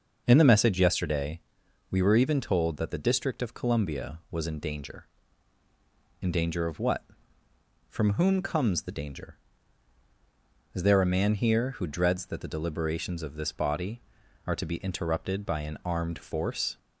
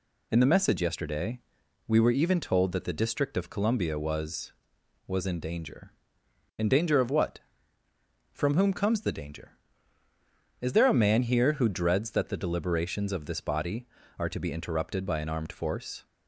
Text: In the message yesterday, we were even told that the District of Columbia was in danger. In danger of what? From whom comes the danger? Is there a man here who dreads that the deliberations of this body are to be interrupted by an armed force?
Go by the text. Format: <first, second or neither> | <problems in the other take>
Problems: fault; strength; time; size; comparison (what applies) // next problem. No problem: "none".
first | says "was" twice; at 5.0 s